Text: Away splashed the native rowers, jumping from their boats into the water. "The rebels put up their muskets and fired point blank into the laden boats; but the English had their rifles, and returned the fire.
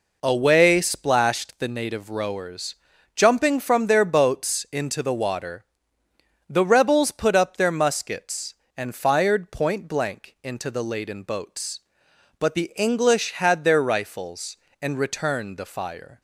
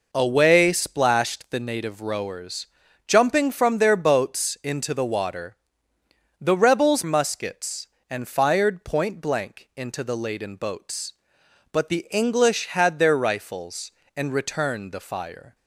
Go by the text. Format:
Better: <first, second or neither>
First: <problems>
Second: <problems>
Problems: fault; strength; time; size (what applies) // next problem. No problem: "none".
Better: first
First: none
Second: skips "put up their"; at 7.0 s